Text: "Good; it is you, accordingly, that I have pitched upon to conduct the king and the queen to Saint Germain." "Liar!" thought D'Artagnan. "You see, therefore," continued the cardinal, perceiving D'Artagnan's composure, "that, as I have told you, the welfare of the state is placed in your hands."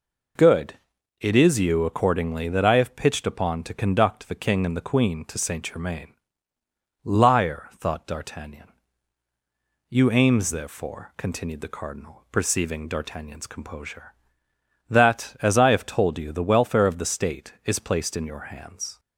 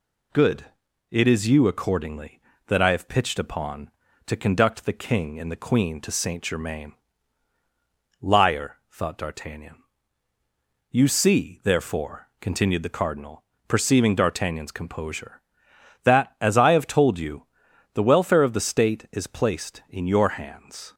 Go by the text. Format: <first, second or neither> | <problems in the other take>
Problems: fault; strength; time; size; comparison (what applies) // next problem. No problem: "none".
second | says "aims" for "see"; at 10.1 s